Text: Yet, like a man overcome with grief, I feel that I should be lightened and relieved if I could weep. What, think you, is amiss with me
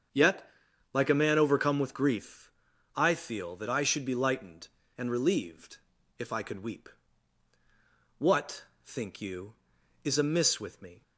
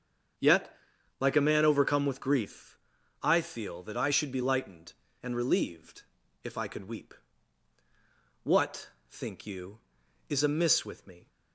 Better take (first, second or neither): neither